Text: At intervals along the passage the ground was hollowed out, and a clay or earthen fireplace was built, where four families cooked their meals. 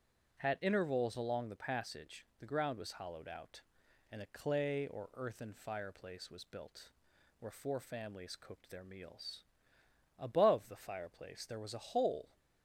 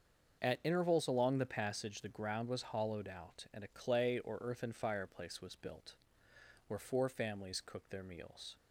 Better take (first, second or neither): second